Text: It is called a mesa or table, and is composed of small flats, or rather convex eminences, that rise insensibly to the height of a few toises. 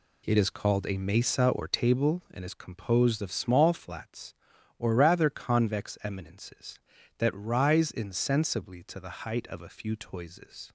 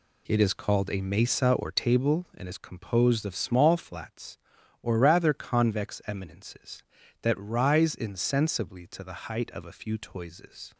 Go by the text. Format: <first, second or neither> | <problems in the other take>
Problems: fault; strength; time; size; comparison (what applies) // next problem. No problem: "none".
neither | none